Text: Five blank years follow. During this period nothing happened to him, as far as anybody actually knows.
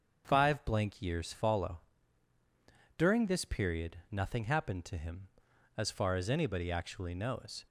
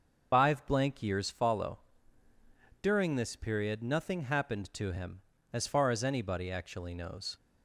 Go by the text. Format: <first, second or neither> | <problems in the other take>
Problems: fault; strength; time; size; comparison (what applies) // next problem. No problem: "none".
first | loses the start of "Five"; at 0.3 s; 95 ms // starts louder than the rest; until 1.3 s; 6.5 dB; strong in the first